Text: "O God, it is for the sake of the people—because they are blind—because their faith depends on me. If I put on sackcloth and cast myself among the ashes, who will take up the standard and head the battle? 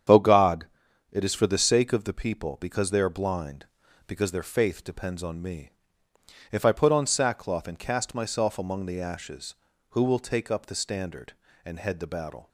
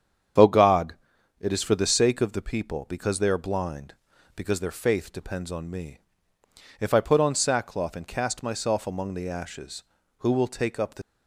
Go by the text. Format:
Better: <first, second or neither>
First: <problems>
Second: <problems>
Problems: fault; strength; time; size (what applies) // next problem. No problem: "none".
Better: first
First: starts louder than the rest; strong; until 1.5 s; 8.5 dB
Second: starts louder than the rest; strong; until 1.8 s; 8 dB // stops before "standard and head the battle"; at 11.0 s